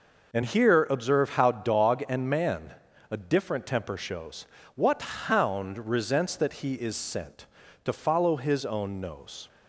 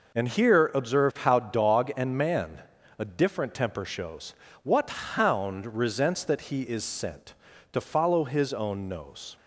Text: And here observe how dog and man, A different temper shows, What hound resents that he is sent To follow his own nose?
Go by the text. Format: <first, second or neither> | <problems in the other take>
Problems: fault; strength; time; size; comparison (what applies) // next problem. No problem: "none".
neither | none